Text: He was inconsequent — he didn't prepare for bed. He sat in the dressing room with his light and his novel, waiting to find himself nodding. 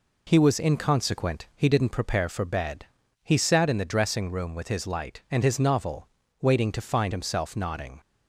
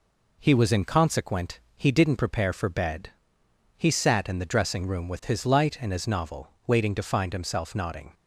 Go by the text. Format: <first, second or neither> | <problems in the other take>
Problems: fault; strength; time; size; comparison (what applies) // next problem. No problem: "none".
neither | none